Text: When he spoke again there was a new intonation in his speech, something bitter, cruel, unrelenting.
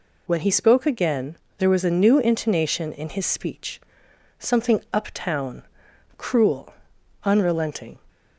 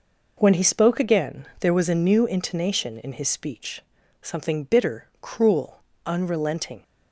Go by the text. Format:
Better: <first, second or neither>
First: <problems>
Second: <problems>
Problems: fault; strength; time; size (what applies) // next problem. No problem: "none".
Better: second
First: pauses between "again" and "there"; slight; at 1.3 s; 0.22 s long // says "uptown" for "bitter"; at 4.8 s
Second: none